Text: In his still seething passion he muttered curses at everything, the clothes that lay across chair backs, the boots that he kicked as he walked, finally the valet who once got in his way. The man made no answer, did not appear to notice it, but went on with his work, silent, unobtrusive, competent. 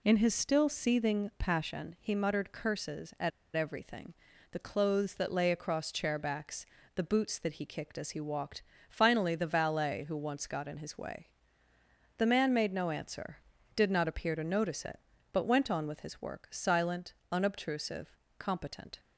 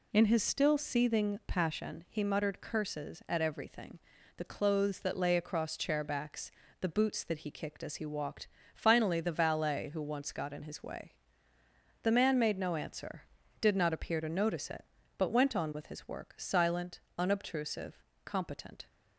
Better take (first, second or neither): second